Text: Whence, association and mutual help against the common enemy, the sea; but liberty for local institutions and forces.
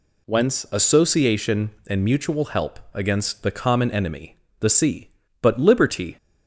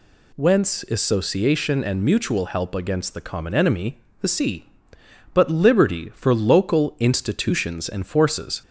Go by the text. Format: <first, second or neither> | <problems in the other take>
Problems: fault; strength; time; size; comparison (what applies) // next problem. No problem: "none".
second | stops before "for local institutions and forces"; at 6.1 s